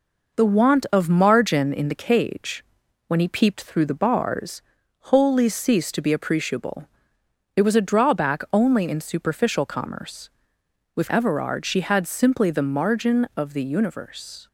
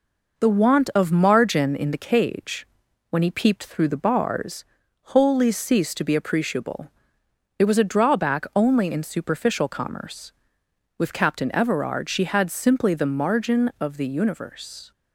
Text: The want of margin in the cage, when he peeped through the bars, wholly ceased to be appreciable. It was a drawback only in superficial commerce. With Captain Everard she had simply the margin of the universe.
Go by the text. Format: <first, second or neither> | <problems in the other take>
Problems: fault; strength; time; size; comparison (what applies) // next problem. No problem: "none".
second | skips "Captain"; at 11.1 s